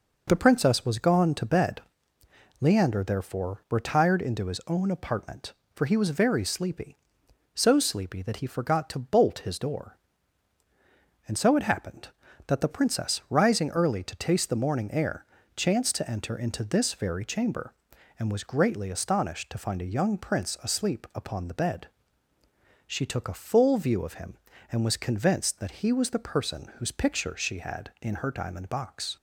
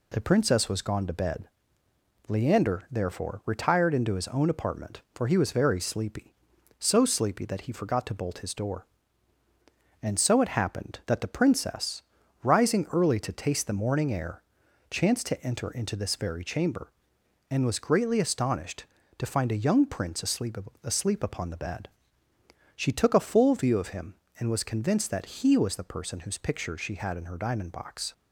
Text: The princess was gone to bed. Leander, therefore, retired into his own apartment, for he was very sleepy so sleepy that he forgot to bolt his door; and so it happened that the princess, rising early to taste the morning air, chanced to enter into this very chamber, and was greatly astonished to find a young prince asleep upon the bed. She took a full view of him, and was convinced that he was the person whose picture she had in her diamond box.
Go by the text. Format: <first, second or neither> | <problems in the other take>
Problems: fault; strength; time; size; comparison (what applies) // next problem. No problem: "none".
first | says "asleep" twice; at 20.8 s